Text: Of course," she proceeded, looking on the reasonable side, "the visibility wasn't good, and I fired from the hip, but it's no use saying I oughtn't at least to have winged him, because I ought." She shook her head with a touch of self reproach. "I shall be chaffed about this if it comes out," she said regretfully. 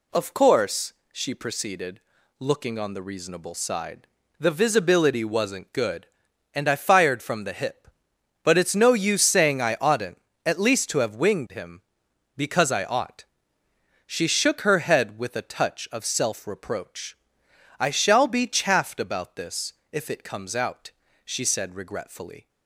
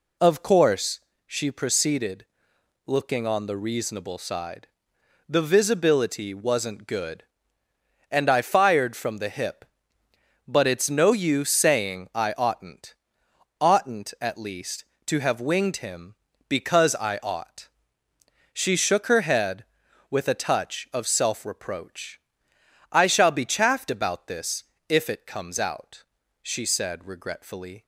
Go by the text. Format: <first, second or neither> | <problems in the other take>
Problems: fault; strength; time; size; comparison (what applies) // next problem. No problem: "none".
first | says "oughtn't" twice; at 13.5 s // pauses between "this" and "if"; slight; at 24.6 s; 0.26 s long; slight in the first